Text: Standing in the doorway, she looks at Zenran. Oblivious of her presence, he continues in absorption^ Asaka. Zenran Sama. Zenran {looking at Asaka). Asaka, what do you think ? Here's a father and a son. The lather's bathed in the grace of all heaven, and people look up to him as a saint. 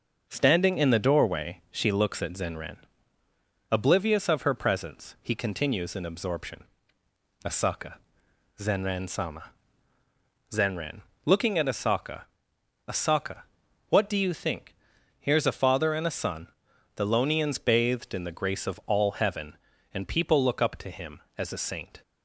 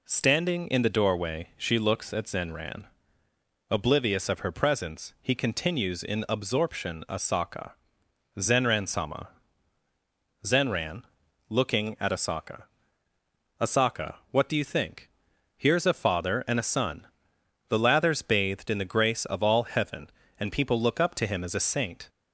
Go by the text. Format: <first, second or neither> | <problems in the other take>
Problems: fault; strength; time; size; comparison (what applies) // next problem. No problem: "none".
second | pauses between "absorption" and "Asaka"; noticeable; at 6.6 s; 0.80 s long // says "lonians" for "lather's"; at 17.0 s